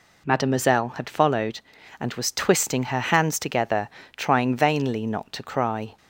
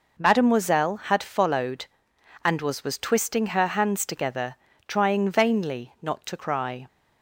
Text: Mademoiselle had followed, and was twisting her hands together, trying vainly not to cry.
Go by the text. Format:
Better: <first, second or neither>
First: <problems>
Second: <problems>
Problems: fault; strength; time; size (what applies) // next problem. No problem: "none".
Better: first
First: none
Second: says "was" twice; at 2.8 s